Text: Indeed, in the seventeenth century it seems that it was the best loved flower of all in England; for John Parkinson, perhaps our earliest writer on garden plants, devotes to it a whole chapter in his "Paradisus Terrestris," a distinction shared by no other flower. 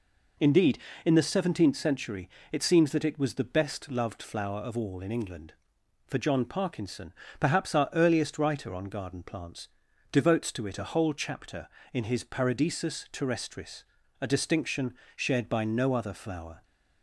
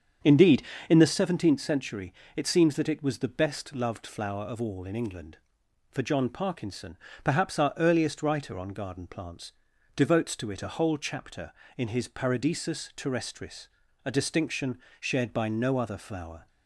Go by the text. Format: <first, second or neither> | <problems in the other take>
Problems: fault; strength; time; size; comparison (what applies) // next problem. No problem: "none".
first | starts louder than the rest; strong; until 1.3 s; 7.5 dB // pauses between "century" and "it"; slight; at 2.1 s; 0.22 s long; slight in the first // pauses between "distinction" and "shared"; slight; at 14.7 s; 0.22 s long; slight in the first